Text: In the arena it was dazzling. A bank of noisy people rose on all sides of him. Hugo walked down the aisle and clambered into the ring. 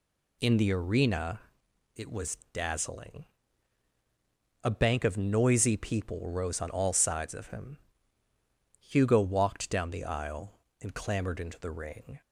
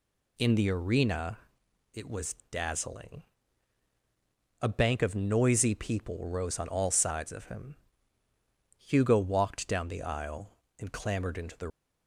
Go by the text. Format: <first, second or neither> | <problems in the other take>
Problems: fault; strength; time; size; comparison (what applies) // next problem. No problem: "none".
first | pauses between "arena" and "it"; noticeable; at 1.3 s; 0.56 s long; noticeable in the first // pauses between "was" and "dazzling"; slight; at 2.3 s; 0.16 s long; slight in the first // stops before "ring"; at 11.6 s